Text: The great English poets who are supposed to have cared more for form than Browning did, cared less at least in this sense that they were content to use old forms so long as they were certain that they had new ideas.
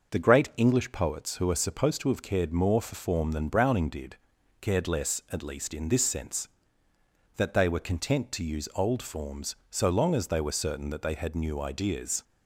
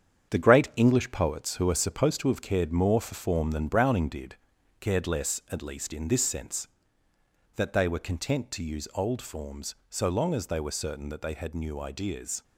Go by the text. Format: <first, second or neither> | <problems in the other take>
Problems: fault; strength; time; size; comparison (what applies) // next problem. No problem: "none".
first | gets quieter; strong; throughout; 7.5 dB